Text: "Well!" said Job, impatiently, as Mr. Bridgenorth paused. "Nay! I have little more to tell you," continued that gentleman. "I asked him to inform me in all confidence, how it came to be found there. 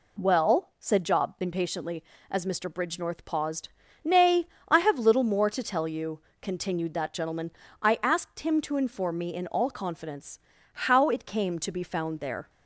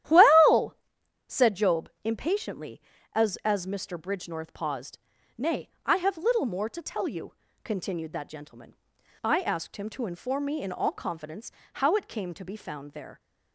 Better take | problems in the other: first | starts louder than the rest; strong; until 1.6 s; 12 dB // says "as" twice; at 3.4 s

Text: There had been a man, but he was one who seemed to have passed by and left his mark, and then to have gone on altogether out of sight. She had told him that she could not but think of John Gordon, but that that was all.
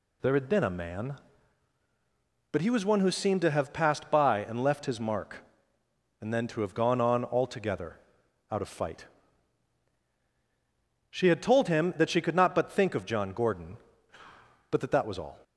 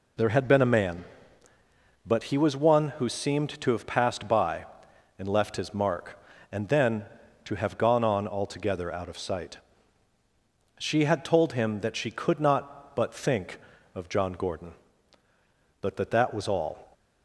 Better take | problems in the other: second | pauses between "altogether" and "out"; noticeable; at 7.9 s; 0.52 s long // says "fight" for "sight"; at 8.6 s

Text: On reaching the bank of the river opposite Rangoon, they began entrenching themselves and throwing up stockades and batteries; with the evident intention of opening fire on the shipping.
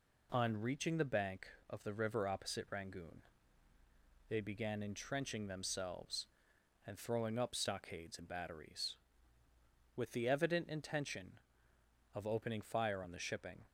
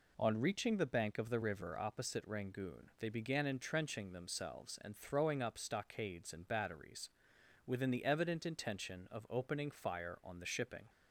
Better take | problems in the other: first | says "within" for "with"; at 7.6 s

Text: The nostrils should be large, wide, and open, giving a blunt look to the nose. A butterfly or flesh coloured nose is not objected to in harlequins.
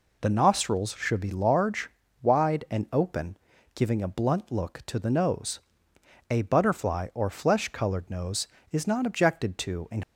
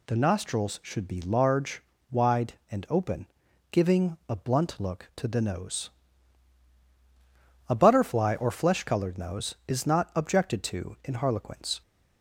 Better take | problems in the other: second | stops before "harlequins"; at 10.0 s

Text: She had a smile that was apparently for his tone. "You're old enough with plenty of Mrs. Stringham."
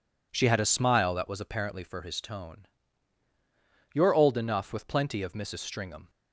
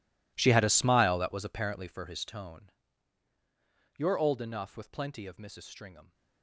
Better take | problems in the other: first | gets quieter; strong; throughout; 19.5 dB

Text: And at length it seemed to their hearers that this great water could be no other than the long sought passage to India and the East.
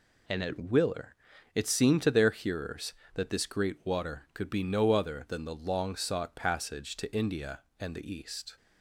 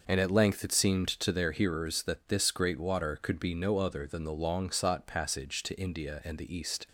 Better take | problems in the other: second | says "willer" for "length"; at 0.5 s

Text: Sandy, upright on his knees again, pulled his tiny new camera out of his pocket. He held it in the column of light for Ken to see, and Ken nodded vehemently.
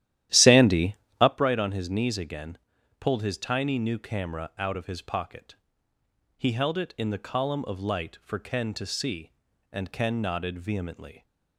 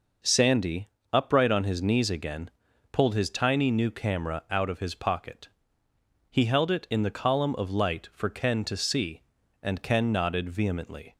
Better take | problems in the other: second | starts louder than the rest; strong; until 1.4 s; 12.5 dB

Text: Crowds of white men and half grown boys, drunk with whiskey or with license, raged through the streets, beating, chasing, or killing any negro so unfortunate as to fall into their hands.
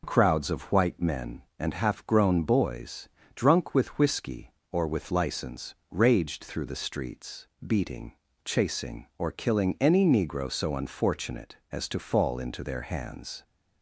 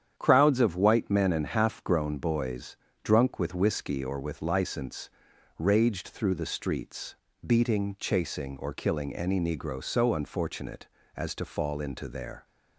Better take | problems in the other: first | starts louder than the rest; strong; until 1.1 s; 9 dB // stops before "hands"; at 12.4 s

